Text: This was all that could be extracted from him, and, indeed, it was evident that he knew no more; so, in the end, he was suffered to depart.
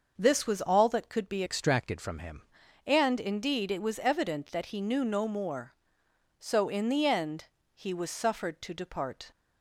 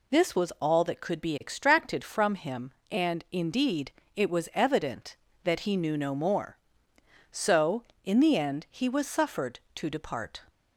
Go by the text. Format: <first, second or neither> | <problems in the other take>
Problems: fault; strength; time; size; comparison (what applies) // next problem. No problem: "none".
second | starts louder than the rest; until 1.2 s; 6 dB // changes voice from "extracted" to "him"; from 1.4 to 2.4 s; 1.0 s long